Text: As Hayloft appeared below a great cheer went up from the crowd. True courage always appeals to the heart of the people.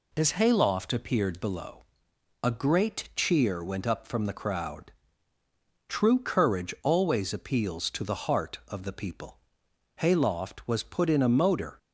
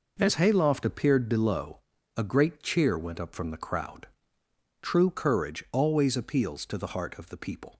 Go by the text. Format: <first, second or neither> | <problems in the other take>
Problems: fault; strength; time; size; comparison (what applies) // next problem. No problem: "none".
second | pauses between "below" and "a"; noticeable; at 1.8 s; 0.60 s long; also in the second // goes on to say "Hayloft was put in a motor"; strong; from 9.9 s on; 1.8 s long